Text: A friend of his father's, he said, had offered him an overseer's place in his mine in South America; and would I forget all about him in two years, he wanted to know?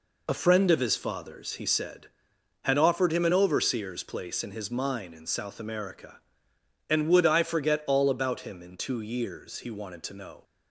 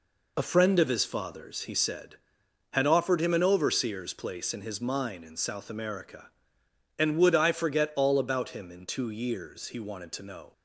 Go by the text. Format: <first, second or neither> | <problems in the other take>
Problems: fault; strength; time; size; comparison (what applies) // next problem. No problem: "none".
neither | none